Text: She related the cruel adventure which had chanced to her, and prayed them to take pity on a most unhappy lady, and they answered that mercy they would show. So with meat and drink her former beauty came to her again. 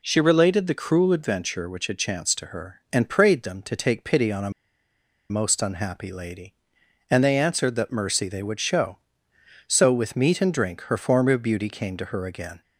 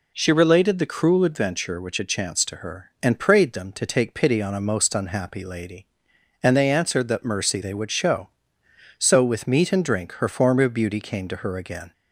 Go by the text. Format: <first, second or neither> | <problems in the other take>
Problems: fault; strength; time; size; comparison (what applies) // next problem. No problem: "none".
second | pauses between "a" and "most"; noticeable; at 4.4 s; 0.80 s long